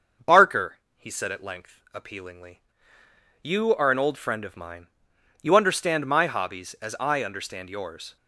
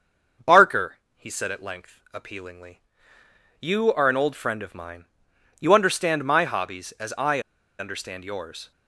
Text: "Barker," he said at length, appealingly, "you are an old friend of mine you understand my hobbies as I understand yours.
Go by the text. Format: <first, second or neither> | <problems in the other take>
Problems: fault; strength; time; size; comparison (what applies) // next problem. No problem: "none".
first | starts louder than the rest; until 1.6 s; 6.5 dB; also in the first // pauses between "mine" and "you"; noticeable; at 5.0 s; 0.56 s long; noticeable in the first // pauses between "I" and "understand"; at 7.3 s; 0.39 s long